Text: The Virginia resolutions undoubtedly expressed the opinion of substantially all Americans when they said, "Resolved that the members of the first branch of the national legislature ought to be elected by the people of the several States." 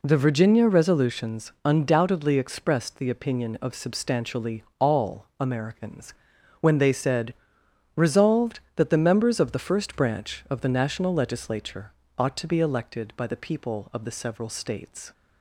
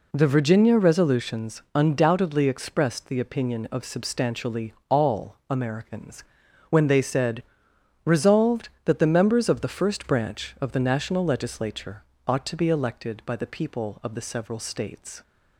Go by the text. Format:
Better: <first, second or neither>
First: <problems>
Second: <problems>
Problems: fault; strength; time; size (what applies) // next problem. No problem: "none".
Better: neither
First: pauses between "substantially" and "all"; slight; at 4.6 s; 0.16 s long // pauses between "Americans" and "when"; at 6.1 s; 0.44 s long // pauses between "legislature" and "ought"; slight; at 11.9 s; 0.26 s long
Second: pauses between "substantially" and "all"; slight; at 4.7 s; 0.16 s long // pauses between "Americans" and "when"; at 6.2 s; 0.44 s long // pauses between "legislature" and "ought"; slight; at 12.0 s; 0.24 s long